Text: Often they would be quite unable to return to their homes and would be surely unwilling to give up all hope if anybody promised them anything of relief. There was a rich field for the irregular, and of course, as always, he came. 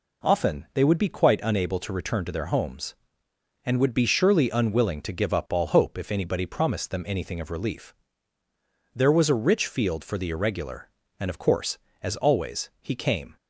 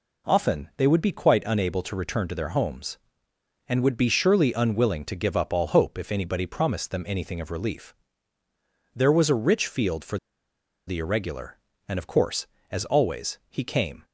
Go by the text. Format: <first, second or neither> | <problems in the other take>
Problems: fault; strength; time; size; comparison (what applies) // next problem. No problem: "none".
first | pauses between "for" and "the"; noticeable; at 10.1 s; 0.69 s long